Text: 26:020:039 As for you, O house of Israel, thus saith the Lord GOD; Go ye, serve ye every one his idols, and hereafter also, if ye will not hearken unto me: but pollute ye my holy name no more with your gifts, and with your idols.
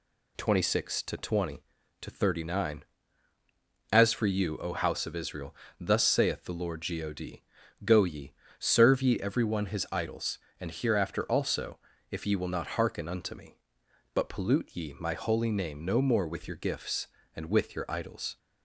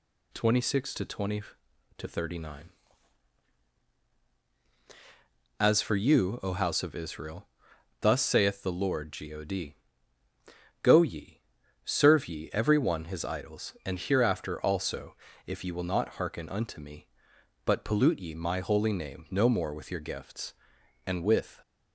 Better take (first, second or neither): first